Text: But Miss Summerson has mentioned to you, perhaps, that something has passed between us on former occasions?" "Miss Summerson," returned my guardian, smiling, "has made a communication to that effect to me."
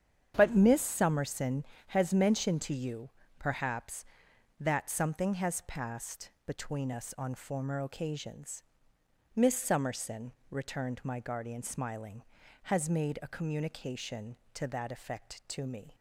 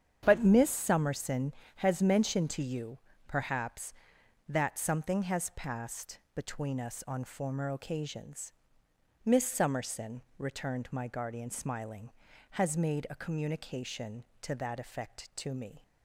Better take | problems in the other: neither | starts louder than the rest; strong; the same in both // pauses between "passed" and "between"; slight; the same in both

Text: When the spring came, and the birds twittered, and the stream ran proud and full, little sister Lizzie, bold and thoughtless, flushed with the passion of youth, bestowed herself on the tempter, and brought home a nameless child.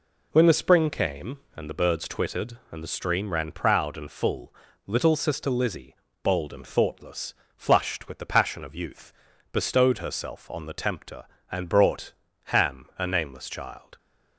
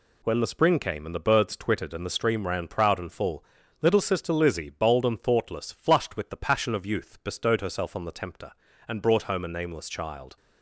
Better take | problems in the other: second | says "ham" for "home"; at 12.4 s

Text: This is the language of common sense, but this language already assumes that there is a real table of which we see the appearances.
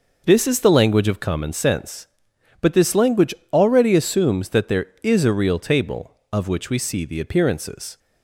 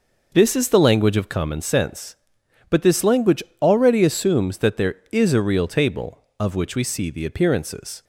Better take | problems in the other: neither | pauses between "language" and "already"; slight; the same in both

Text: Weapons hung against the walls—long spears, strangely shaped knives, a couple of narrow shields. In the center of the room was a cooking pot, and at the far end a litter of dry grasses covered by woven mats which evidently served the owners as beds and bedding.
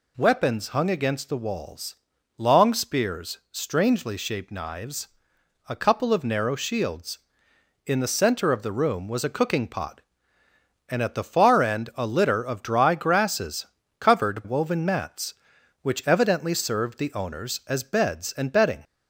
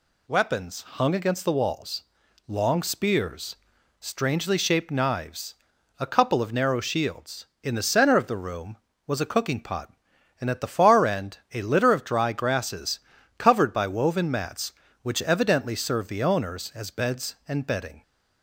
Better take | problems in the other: second | pauses between "grasses" and "covered"; slight; at 13.6 s; 0.32 s long; also in the second // skips "by"; at 14.4 s

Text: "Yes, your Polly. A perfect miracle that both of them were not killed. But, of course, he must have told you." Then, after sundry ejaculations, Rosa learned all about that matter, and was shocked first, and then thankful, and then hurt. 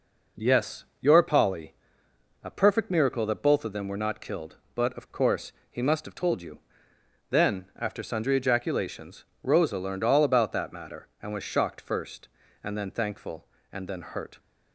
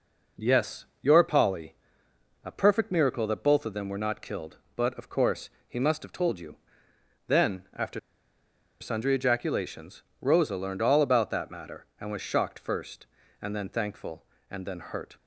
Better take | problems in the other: first | pauses between "after" and "sundry"; noticeable; at 7.9 s; 0.81 s long

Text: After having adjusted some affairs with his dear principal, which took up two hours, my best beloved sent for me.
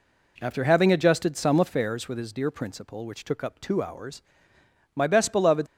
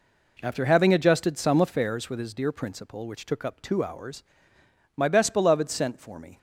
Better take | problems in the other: second | stops before "sent for me"; at 5.6 s

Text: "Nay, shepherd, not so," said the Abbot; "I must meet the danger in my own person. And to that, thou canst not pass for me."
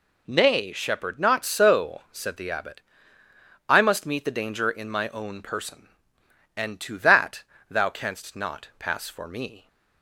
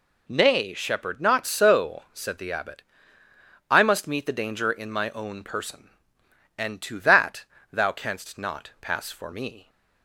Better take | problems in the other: neither | none

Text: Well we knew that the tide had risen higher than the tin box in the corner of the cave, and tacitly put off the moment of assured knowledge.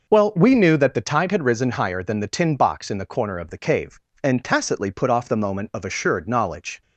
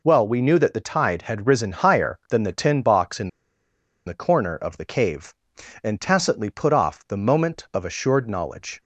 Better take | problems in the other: first | pauses between "in" and "the"; noticeable; at 3.2 s; 0.76 s long

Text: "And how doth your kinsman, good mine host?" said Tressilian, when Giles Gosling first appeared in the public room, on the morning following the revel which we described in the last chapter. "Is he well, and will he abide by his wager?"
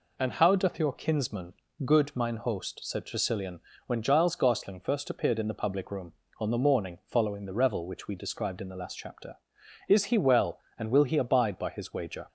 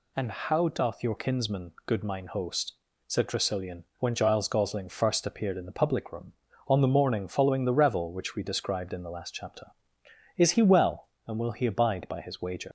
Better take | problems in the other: first | leaves "wager" unfinished; at 12.6 s; 85 ms

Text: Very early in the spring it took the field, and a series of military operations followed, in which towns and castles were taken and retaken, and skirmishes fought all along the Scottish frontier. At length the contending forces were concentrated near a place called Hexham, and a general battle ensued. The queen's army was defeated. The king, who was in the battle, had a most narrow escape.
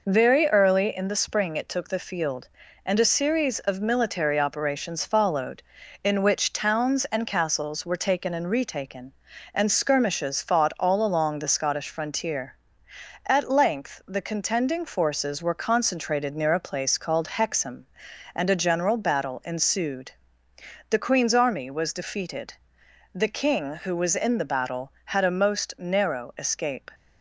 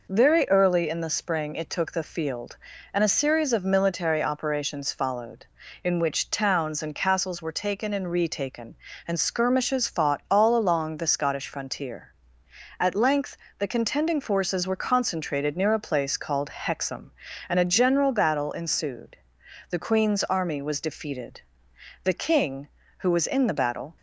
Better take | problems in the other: first | pauses between "length" and "the"; slight; at 13.3 s; 0.18 s long // stops before "had a most narrow escape"; at 23.9 s

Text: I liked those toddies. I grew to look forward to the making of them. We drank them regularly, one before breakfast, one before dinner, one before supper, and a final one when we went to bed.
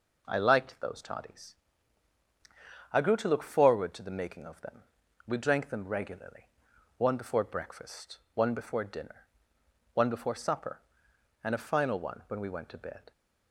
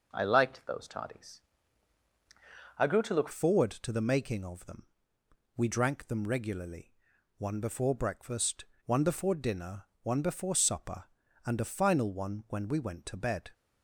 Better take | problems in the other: first | changes voice at "forward"; from 3.3 s on; 10.2 s long

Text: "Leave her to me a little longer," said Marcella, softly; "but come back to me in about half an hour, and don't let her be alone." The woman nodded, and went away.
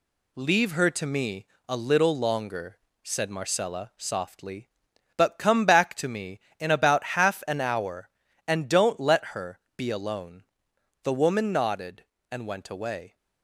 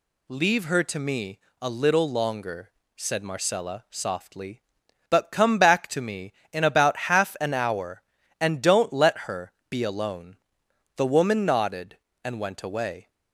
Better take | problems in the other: second | gets quieter; noticeable; throughout; 5 dB // pauses between "me" and "a"; slight; at 1.4 s; 0.22 s long; slight in the second // pauses between "her" and "be"; slight; at 9.5 s; 0.16 s long; slight in the second

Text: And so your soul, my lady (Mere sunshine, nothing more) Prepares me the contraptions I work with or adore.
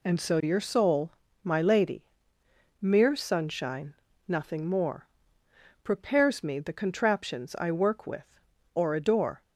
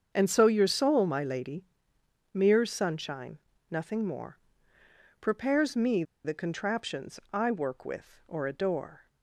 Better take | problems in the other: first | starts louder than the rest; until 1.1 s; 7 dB // pauses between "me" and "the"; slight; at 6.0 s; 0.22 s long

